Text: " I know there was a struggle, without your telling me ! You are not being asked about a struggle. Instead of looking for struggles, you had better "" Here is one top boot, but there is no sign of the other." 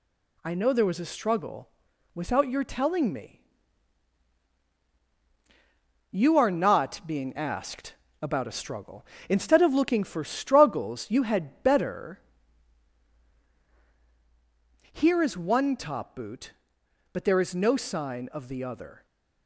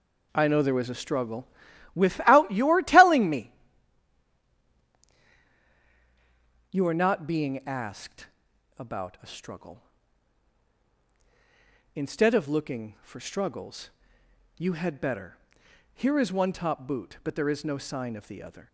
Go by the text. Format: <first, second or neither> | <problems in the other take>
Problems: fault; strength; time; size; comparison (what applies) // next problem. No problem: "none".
first | starts louder than the rest; noticeable; until 2.0 s; 4 dB // pauses between "asked" and "about"; noticeable; at 8.2 s; 0.50 s long; slight in the first